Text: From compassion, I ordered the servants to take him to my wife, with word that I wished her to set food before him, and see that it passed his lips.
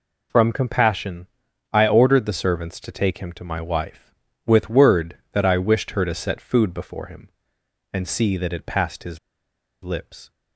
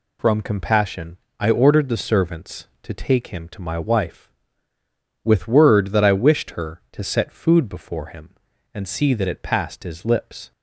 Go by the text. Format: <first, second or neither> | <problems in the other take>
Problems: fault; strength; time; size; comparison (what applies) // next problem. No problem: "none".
second | pauses between "his" and "lips"; noticeable; at 9.1 s; 0.63 s long